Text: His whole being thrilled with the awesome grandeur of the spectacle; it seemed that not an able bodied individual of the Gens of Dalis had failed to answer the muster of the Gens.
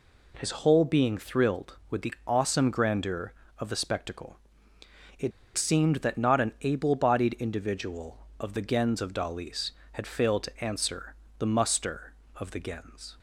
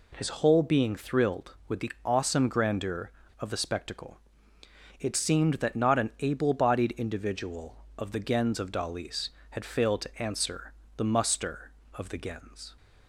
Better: second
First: pauses between "it" and "seemed"; slight; at 5.3 s; 0.25 s long // pauses between "answer" and "the"; slight; at 11.1 s; 0.24 s long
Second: pauses between "answer" and "the"; slight; at 10.7 s; 0.24 s long

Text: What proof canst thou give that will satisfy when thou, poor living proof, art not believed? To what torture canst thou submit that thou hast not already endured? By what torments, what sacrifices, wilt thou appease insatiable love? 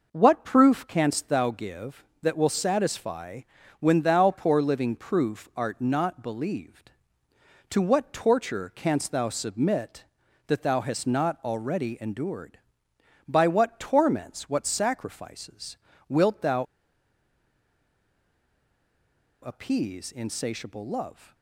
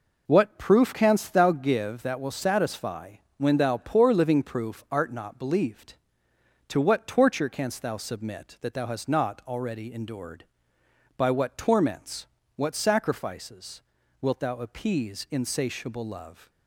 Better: second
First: pauses between "satisfy" and "when"; slight; at 3.4 s; 0.36 s long // pauses between "thou" and "appease"; strong; at 16.6 s; 2.7 s long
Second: pauses between "satisfy" and "when"; slight; at 3.1 s; 0.20 s long

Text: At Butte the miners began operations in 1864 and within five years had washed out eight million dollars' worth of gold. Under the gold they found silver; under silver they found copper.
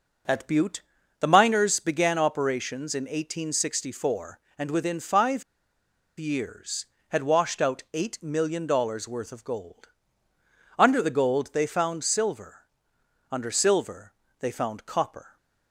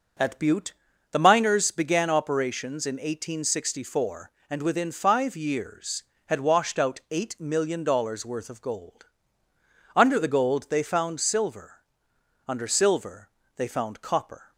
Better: second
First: pauses between "Butte" and "the"; at 0.8 s; 0.38 s long // pauses between "five" and "years"; noticeable; at 5.4 s; 0.75 s long // pauses between "silver" and "they"; slight; at 14.1 s; 0.28 s long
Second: pauses between "Butte" and "the"; at 0.7 s; 0.38 s long // pauses between "silver" and "they"; slight; at 13.2 s; 0.28 s long

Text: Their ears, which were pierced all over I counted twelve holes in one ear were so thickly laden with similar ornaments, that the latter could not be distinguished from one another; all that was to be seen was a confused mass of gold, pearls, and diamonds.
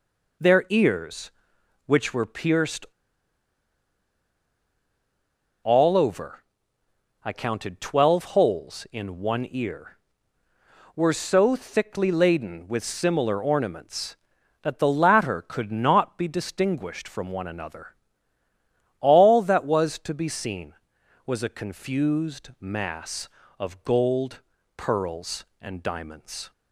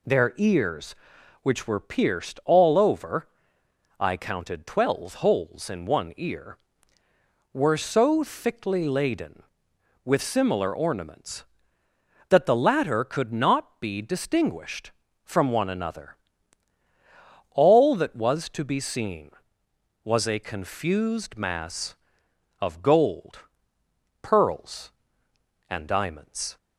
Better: second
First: pauses between "pierced" and "all"; strong; at 2.8 s; 2.7 s long // pauses between "over" and "I"; noticeable; at 6.3 s; 0.86 s long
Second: pauses between "over" and "I"; noticeable; at 3.2 s; 0.72 s long

